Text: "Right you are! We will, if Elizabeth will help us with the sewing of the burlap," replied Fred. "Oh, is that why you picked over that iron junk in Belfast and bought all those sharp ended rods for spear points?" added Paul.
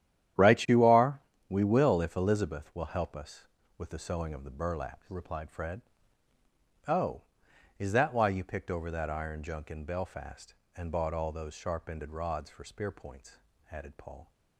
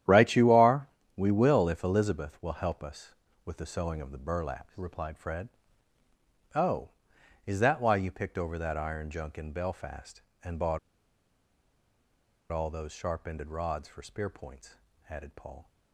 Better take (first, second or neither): first